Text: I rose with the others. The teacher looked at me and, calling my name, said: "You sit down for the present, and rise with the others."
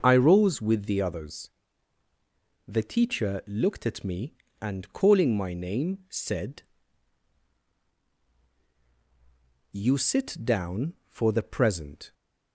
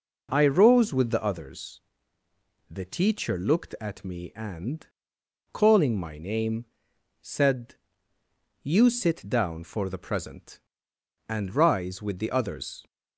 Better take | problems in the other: second | starts louder than the rest; until 1.0 s; 6.5 dB // stops before "and rise with the others"; at 12.1 s

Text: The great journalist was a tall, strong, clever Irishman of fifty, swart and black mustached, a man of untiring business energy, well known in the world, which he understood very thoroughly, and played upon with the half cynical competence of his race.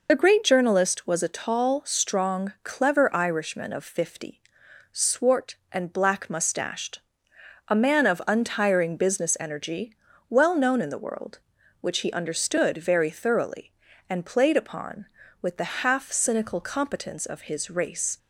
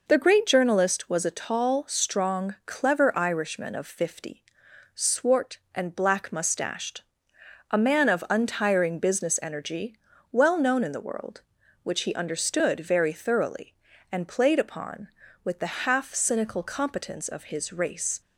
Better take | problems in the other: second | loses the start of "The"; at 0.0 s; 40 ms

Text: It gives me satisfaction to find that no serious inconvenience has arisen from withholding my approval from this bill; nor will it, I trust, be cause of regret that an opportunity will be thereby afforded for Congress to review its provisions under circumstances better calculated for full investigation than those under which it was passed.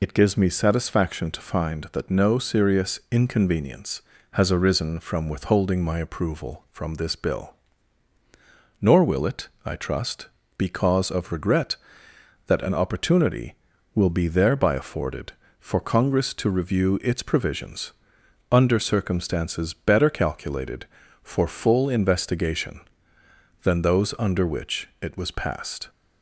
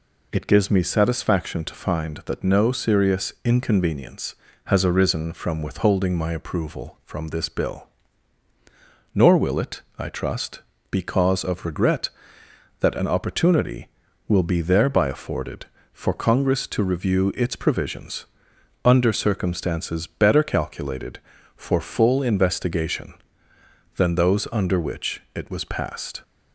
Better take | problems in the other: second | loses the start of "It"; at 0.0 s; 25 ms // pauses between "provisions" and "under"; noticeable; at 17.9 s; 0.60 s long; noticeable in the second

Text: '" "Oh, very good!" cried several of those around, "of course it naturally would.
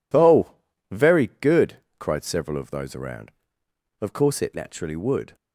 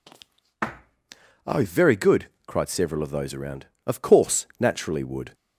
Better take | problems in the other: first | skips "it"; at 4.5 s

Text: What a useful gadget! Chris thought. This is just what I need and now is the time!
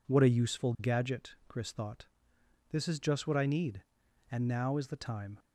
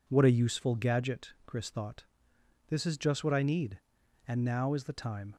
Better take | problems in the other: neither | none

